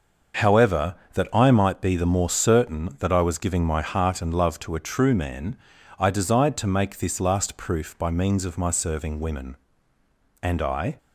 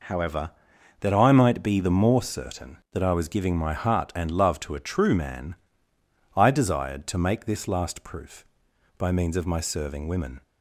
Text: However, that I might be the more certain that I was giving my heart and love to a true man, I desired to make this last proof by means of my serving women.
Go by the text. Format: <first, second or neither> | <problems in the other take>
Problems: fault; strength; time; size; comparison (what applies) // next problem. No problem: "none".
second | starts louder than the rest; until 1.6 s; 6 dB // goes on to say "And I"; from 10.4 s on; 0.54 s long